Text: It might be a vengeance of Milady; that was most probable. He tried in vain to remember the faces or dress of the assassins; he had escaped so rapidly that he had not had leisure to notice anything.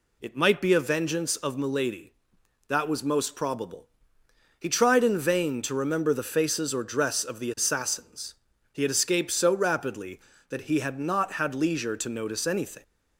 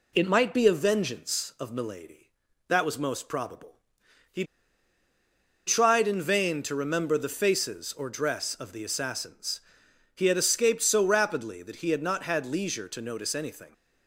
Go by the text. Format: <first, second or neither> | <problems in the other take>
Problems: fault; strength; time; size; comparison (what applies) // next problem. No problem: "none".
first | pauses between "He" and "tried"; at 4.4 s; 1.2 s long